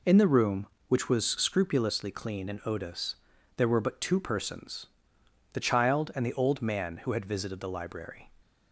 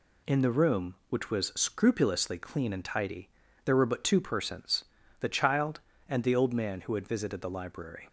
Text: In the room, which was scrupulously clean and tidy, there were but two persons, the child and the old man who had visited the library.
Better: second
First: says "odous" for "tidy"; at 2.6 s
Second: none

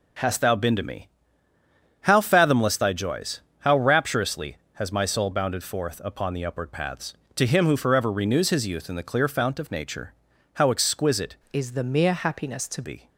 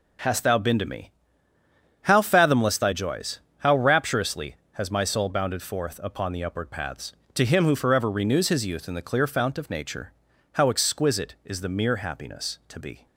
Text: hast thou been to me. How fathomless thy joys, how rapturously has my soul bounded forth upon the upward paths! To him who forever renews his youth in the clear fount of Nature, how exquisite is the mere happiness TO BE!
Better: second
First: changes voice from "is" to "TO"; from 11.5 to 12.8 s; 1.3 s long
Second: none

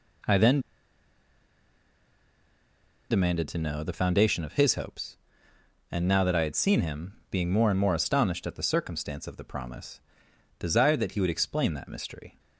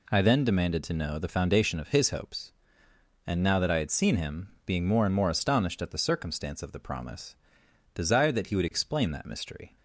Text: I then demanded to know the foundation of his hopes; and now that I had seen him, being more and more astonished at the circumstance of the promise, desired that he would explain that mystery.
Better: second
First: pauses between "then" and "demanded"; strong; at 0.5 s; 2.5 s long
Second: none

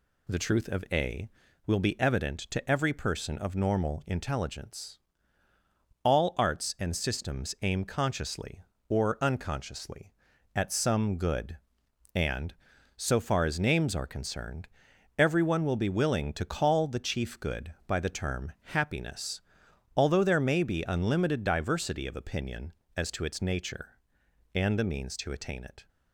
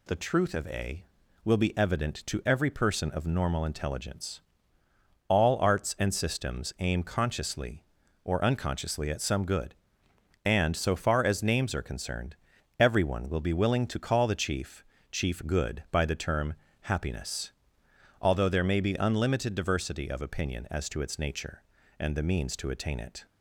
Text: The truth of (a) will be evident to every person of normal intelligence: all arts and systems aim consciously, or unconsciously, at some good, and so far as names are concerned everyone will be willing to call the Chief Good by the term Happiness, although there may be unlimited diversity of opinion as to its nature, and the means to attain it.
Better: first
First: pauses between "concerned" and "everyone"; noticeable; at 14.6 s; 0.50 s long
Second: pauses between "concerned" and "everyone"; at 12.3 s; 0.42 s long // says "Chief" twice; at 15.1 s // pauses between "term" and "Happiness"; slight; at 16.5 s; 0.30 s long

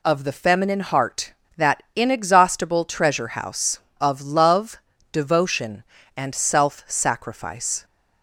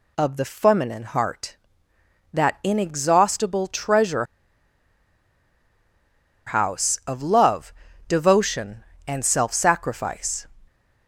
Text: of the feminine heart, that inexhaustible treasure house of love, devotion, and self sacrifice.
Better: first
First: none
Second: pauses between "treasure" and "house"; strong; at 4.2 s; 2.2 s long

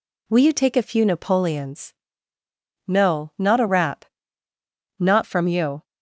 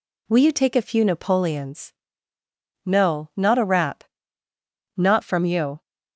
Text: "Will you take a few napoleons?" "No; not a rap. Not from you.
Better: neither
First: none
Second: none

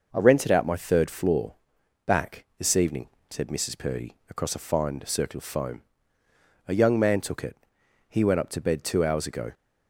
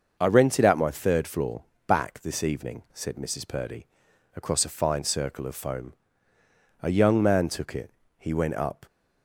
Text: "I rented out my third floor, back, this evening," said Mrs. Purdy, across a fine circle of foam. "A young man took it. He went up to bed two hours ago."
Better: first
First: none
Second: starts louder than the rest; noticeable; until 1.2 s; 6 dB // stops before "to bed two hours ago"; at 8.8 s

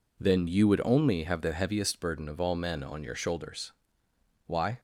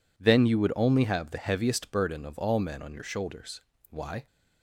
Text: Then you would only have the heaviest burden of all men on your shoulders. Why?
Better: neither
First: none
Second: none

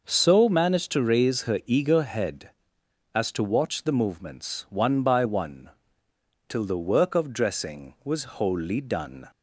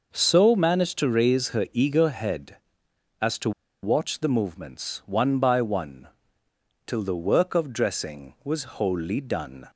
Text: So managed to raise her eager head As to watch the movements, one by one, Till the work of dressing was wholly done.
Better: first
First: none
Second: pauses between "to" and "watch"; slight; at 3.5 s; 0.32 s long

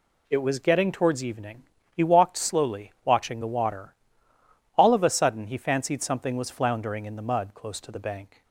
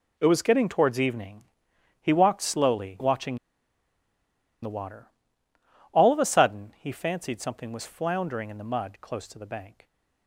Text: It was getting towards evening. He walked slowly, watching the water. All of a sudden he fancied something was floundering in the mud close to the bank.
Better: first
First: none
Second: pauses between "watching" and "the"; strong; at 3.3 s; 1.2 s long

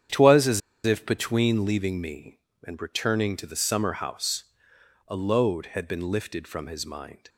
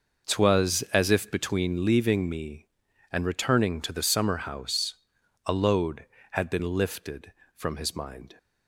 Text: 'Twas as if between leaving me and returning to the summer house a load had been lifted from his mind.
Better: second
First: starts louder than the rest; strong; until 1.3 s; 8.5 dB // pauses between "as" and "if"; slight; at 0.6 s; 0.24 s long // pauses between "house" and "a"; noticeable; at 4.4 s; 0.64 s long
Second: pauses between "house" and "a"; noticeable; at 4.9 s; 0.50 s long

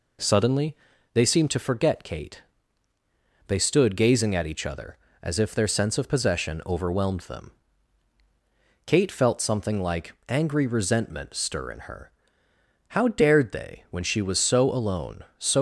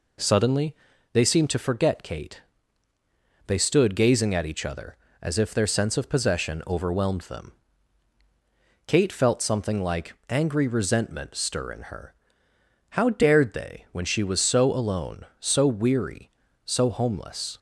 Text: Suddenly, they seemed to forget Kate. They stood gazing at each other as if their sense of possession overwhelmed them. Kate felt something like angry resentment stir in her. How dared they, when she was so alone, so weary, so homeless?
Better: second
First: pauses between "like" and "angry"; slight; at 10.1 s; 0.16 s long // stops before "weary so homeless"; at 15.5 s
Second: pauses between "like" and "angry"; slight; at 10.1 s; 0.16 s long

